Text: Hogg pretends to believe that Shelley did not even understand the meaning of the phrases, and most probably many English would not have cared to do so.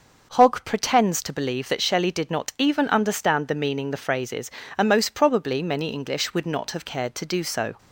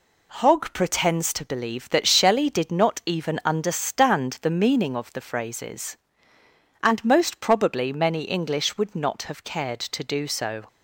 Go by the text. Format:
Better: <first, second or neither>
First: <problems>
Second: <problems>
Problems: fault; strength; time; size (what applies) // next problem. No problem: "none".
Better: second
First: starts louder than the rest; noticeable; until 1.3 s; 6 dB // skips "of"; at 3.9 s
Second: none